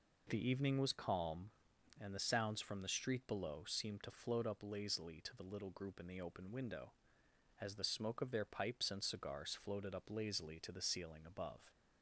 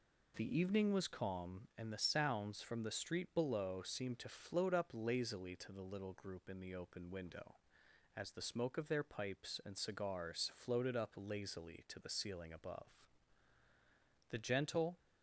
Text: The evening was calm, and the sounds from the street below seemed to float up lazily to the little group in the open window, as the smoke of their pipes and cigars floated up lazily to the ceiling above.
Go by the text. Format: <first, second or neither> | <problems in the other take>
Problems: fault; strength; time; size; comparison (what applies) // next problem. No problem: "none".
first | goes on to say "The gentle"; noticeable; from 14.2 s on; 0.68 s long